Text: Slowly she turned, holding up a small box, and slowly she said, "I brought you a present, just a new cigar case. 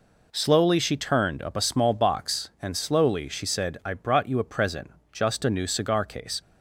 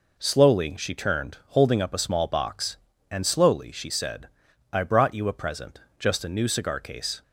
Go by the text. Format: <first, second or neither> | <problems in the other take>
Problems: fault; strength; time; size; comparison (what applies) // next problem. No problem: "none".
second | skips "holding"; at 1.4 s